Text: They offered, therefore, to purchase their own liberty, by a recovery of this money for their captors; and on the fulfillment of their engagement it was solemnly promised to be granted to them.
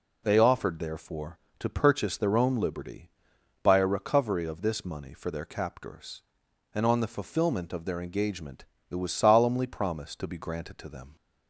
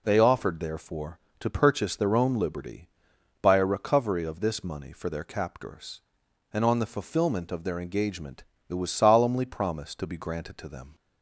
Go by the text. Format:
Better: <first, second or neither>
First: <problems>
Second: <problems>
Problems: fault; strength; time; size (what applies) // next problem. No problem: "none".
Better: neither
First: pauses between "engagement" and "it"; slight; at 8.6 s; 0.24 s long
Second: pauses between "engagement" and "it"; slight; at 8.4 s; 0.24 s long